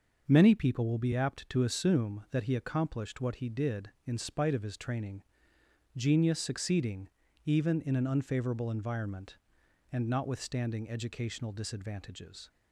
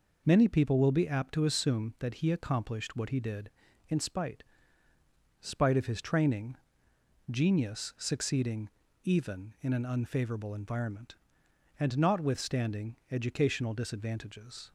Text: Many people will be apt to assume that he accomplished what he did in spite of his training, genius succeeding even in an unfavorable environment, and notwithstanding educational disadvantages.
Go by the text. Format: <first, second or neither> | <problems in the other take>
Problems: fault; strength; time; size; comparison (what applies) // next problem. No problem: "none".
first | says "spite" twice; at 5.4 s // pauses between "succeeding" and "even"; slight; at 8.6 s; 0.34 s long; slight in the first // pauses between "notwithstanding" and "educational"; slight; at 12.9 s; 0.16 s long